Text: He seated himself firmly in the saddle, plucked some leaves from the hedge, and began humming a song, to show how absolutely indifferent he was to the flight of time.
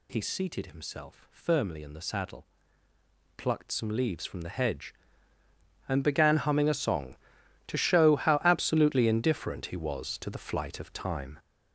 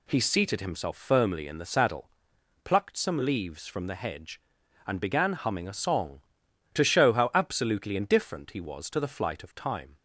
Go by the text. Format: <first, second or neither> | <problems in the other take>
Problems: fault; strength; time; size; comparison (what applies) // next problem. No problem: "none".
second | gets louder; strong; throughout; 7.5 dB